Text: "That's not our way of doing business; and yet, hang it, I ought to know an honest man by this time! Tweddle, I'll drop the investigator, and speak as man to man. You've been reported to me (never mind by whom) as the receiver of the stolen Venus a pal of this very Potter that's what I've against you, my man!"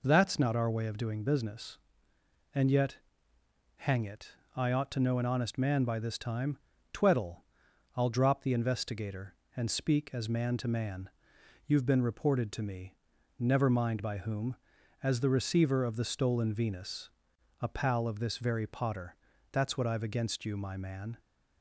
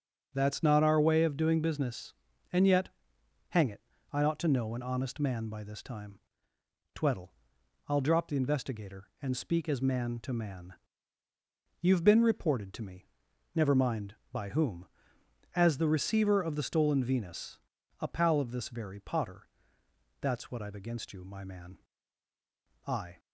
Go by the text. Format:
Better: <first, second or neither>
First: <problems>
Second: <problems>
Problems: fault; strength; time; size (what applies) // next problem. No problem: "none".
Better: first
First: pauses between "Venus" and "a"; noticeable; at 17.1 s; 0.50 s long // pauses between "Potter" and "that's"; slight; at 19.1 s; 0.36 s long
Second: starts louder than the rest; until 1.3 s; 6.5 dB // pauses between "Venus" and "a"; at 17.5 s; 0.42 s long // pauses between "Potter" and "that's"; noticeable; at 19.4 s; 0.72 s long // goes on to say "I"; slight; from 22.8 s on; 0.34 s long